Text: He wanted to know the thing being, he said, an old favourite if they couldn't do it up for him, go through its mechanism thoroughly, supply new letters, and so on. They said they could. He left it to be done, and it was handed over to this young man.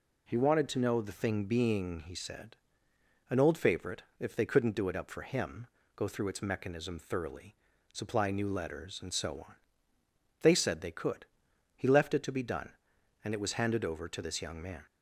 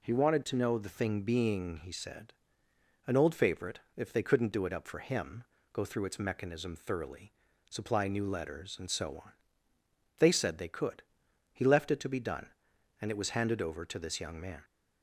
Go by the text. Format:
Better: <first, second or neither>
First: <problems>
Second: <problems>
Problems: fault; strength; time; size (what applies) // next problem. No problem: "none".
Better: neither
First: pauses between "favourite" and "if"; slight; at 4.0 s; 0.16 s long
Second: pauses between "favourite" and "if"; slight; at 3.8 s; 0.16 s long